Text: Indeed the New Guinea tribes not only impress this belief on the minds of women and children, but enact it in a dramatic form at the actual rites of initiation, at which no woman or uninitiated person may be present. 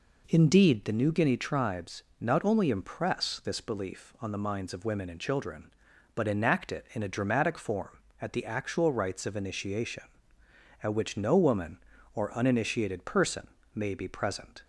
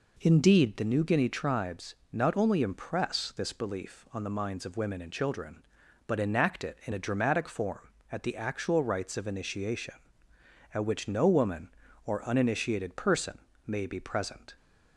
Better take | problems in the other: neither | pauses between "tribes" and "not"; slight; the same in both // pauses between "person" and "may"; slight; the same in both

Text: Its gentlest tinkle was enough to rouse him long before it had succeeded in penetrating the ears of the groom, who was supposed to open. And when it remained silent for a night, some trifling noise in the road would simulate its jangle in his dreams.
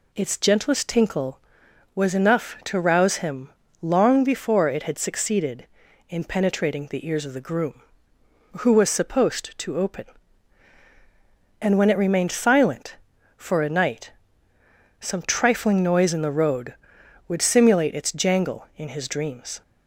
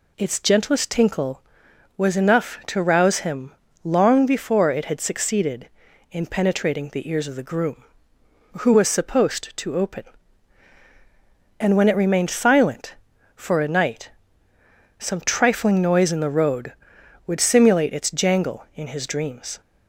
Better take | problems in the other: neither | pauses between "him" and "long"; slight; the same in both

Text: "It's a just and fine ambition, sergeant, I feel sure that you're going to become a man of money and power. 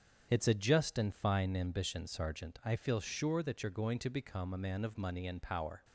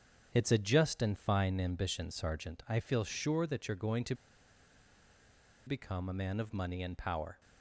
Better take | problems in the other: first | starts louder than the rest; strong; until 1.3 s; 7.5 dB; strong in the first // pauses between "to" and "become"; strong; at 4.1 s; 1.5 s long

